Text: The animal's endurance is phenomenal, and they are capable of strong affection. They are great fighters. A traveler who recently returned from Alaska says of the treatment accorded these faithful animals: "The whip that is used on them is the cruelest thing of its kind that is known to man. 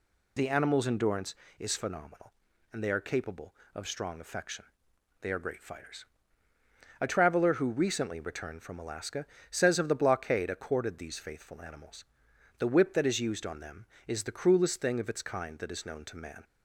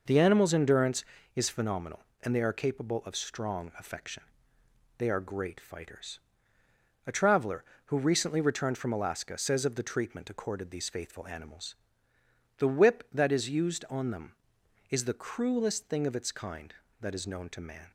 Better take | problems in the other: second | pauses between "Alaska" and "says"; slight; at 9.2 s; 0.24 s long // says "blockade" for "treatment"; at 9.9 s

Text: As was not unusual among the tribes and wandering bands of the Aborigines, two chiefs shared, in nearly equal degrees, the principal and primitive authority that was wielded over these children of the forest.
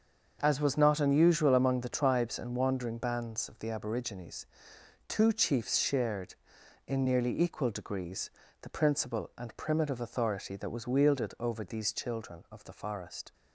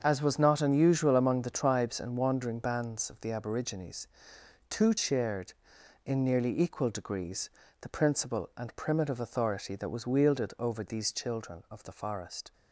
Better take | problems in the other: first | starts louder than the rest; until 1.0 s; 6.5 dB; also in the first // skips "chiefs"; at 4.9 s

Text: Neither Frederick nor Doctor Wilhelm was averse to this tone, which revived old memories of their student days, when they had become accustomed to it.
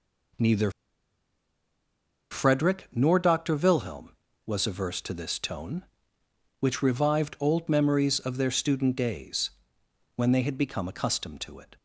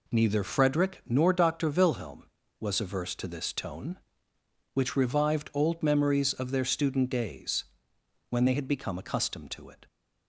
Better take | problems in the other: second | pauses between "Neither" and "Frederick"; strong; at 0.7 s; 1.6 s long

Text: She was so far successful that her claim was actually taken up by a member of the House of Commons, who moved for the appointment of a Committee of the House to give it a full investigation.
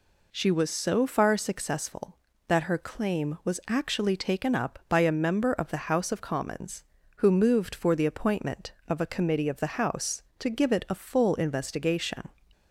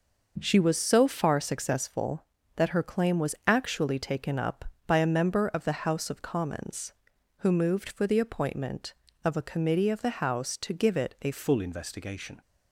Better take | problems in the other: first | changes voice at "full"; from 11.3 s on; 1.1 s long

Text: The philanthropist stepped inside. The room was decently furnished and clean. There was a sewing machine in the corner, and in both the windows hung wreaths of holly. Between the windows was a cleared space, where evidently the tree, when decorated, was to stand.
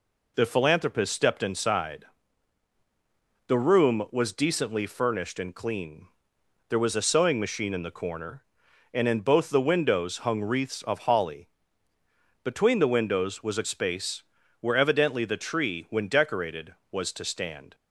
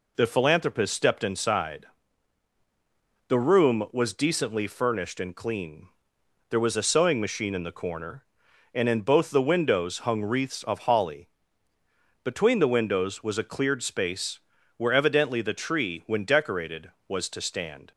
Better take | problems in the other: second | skips "cleared"; at 13.6 s

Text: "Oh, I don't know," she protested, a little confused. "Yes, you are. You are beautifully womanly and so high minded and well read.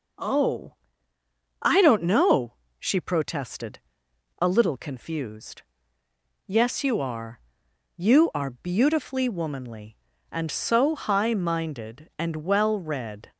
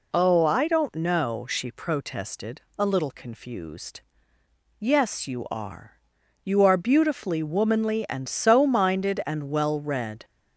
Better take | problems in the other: first | skips "high"; at 8.6 s

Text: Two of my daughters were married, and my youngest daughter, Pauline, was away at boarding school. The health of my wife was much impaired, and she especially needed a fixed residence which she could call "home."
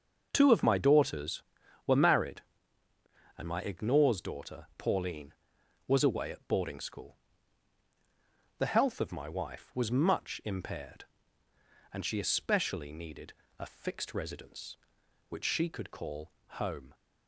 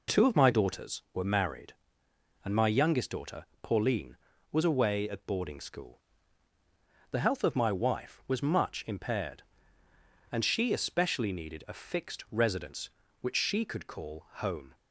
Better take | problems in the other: second | says "ignores" for "youngest"; at 3.6 s // pauses between "needed" and "a"; slight; at 13.3 s; 0.26 s long

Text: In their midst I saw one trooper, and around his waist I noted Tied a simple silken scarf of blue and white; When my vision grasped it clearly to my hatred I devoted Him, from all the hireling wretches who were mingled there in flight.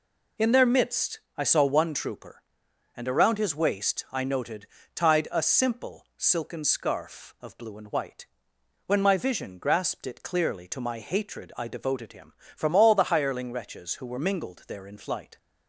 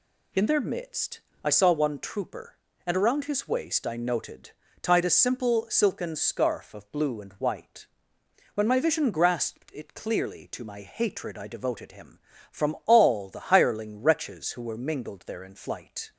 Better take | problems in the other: neither | pauses between "midst" and "I"; slight; the same in both // pauses between "noted" and "Tied"; slight; the same in both

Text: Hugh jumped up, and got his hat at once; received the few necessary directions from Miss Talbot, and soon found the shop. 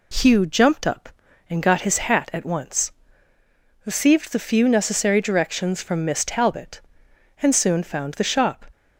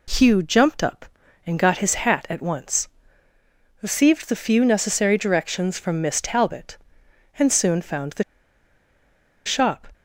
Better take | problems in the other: first | pauses between "the" and "shop"; at 8.2 s; 1.2 s long

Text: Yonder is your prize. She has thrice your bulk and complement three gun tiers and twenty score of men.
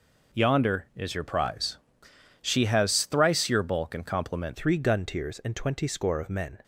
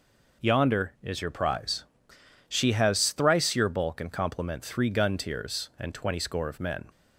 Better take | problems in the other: second | changes voice at "three"; from 4.5 s on; 2.1 s long

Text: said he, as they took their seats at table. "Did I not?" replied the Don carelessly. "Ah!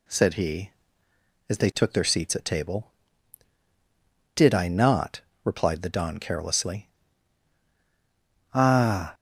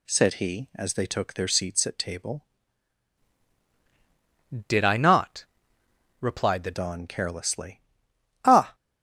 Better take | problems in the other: first | changes voice from "Did" to "the"; from 4.6 to 6.7 s; 2.1 s long

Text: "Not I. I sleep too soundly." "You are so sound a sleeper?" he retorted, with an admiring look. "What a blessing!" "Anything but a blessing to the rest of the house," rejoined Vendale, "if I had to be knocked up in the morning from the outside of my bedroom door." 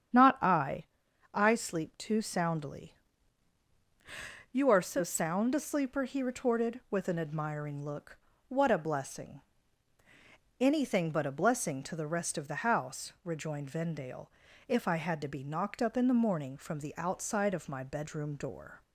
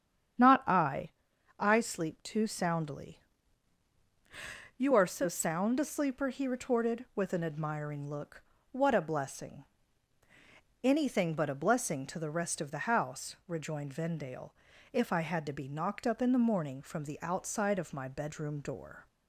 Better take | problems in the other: neither | starts louder than the rest; strong; the same in both

